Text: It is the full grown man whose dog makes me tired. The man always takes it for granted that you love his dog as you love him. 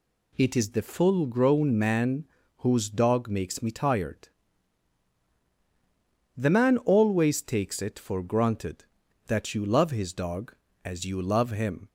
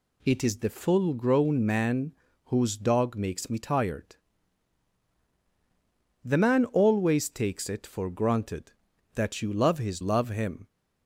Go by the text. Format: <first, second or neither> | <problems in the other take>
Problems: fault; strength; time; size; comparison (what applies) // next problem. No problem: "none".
first | pauses between "man" and "whose"; slight; at 2.1 s; 0.32 s long; slight in the first // skips "dog as you"; at 9.9 s